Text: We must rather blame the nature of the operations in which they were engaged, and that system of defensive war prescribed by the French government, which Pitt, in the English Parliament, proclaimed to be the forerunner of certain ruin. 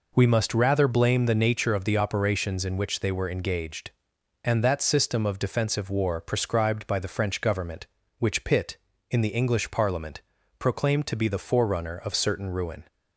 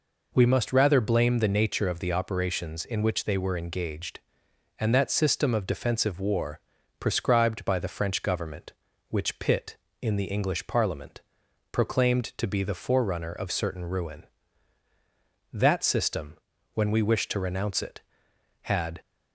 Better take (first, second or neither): first